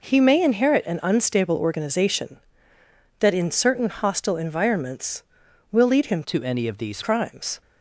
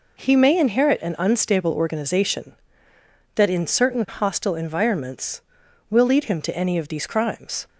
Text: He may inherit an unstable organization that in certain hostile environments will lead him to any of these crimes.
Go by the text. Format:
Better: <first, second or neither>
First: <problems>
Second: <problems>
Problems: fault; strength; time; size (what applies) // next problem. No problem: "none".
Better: second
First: changes voice from "to" to "these"; from 6.2 to 7.0 s; 0.8 s long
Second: none